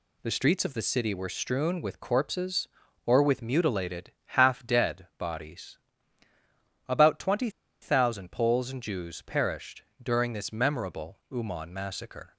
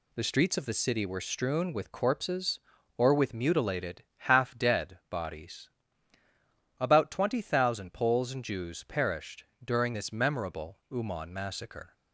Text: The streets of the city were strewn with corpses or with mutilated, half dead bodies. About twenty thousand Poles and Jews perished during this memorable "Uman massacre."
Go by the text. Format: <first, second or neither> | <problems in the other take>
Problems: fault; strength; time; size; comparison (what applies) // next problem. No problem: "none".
second | pauses between "twenty" and "thousand"; slight; at 7.4 s; 0.32 s long // pauses between "perished" and "during"; slight; at 9.8 s; 0.18 s long; slight in the second